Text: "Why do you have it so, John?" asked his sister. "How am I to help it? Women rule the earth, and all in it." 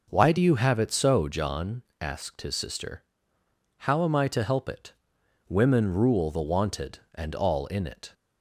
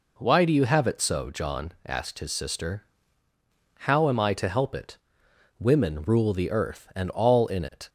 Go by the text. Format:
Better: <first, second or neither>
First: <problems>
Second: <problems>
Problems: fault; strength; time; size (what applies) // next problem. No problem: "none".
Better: second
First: says "wanted" for "earth"; at 6.4 s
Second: none